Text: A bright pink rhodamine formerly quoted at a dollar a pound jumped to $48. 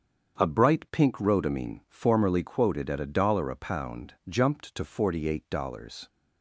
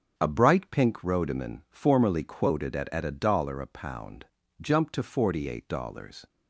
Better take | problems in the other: first | starts louder than the rest; until 1.1 s; 6.5 dB; strong in the first // says "at" twice; at 2.9 s // pauses between "pound" and "jumped"; at 4.2 s; 0.38 s long; slight in the first

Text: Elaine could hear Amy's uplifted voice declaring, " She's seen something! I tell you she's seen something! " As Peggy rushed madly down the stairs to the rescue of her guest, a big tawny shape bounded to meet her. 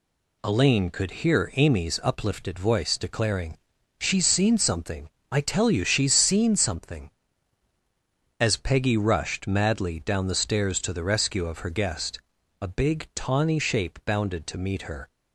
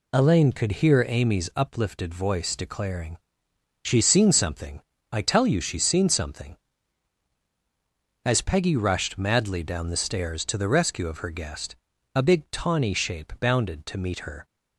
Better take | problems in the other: neither | none

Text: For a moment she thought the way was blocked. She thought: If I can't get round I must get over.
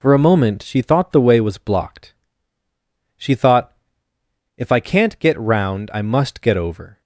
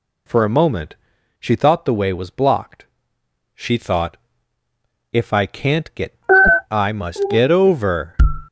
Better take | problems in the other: first | pauses between "moment" and "she"; at 0.9 s; 0.44 s long // skips "round"; at 6.4 s

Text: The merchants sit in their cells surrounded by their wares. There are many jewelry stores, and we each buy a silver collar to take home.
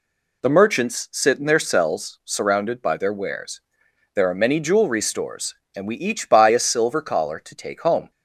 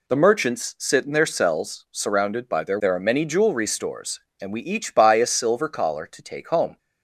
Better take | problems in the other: first | skips "wares"; at 2.7 s

